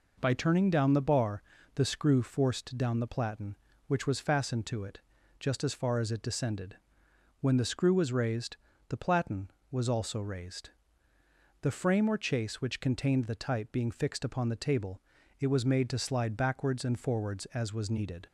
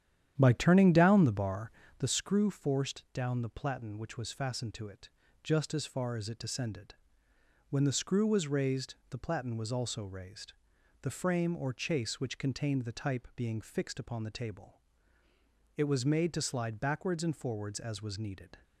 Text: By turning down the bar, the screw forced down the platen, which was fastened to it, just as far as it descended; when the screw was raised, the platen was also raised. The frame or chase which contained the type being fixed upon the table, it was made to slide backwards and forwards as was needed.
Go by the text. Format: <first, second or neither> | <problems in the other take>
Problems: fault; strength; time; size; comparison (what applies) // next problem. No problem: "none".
first | starts louder than the rest; strong; until 2.1 s; 10 dB